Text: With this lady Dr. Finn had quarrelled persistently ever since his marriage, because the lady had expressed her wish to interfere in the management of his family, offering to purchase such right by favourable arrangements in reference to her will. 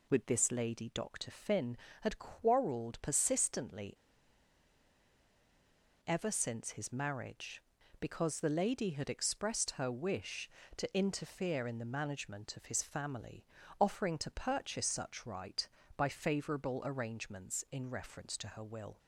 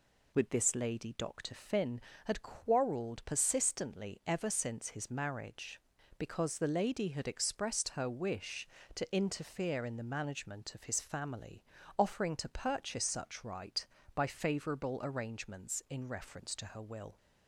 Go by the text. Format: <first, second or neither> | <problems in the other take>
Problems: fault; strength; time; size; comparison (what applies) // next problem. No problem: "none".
second | pauses between "persistently" and "ever"; strong; at 3.9 s; 2.0 s long